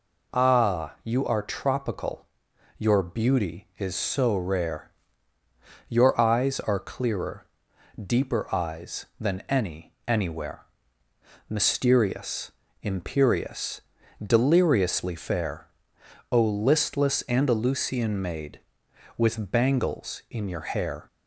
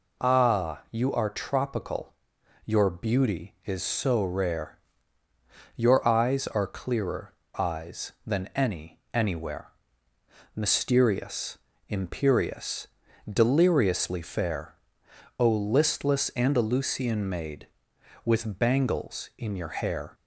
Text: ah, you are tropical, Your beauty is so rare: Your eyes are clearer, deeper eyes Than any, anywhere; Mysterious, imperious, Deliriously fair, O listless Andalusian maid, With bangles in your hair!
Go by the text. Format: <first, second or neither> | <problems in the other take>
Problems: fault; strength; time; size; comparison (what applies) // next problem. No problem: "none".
first | skips "deeper"; at 7.4 s